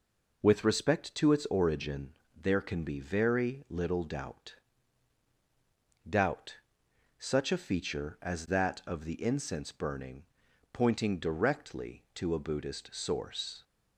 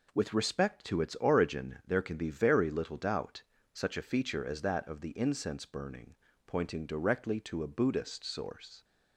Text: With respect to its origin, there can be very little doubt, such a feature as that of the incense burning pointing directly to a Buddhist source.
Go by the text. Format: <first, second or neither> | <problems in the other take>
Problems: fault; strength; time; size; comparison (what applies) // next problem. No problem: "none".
second | says "doubt" twice; at 6.0 s // pauses between "burning" and "pointing"; noticeable; at 10.2 s; 0.50 s long; slight in the second